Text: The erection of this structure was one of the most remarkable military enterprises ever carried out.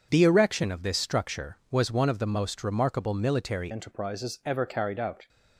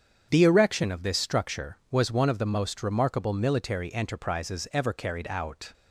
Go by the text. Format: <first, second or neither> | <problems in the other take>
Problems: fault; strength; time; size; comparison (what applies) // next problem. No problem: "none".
second | starts louder than the rest; strong; until 1.1 s; 7 dB; strong in the second // changes voice at "enterprises"; from 3.7 s on; 1.5 s long